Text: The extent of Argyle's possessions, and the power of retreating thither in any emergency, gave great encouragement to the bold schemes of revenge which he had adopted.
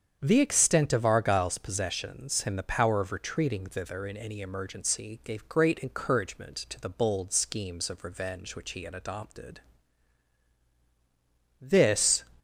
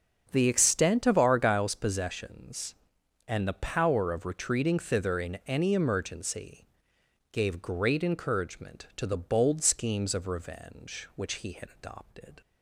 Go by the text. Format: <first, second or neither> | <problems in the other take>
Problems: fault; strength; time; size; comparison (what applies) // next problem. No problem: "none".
second | starts louder than the rest; strong; until 1.2 s; 7.5 dB; also in the second // goes on to say "This"; noticeable; from 11.6 s on; 0.64 s long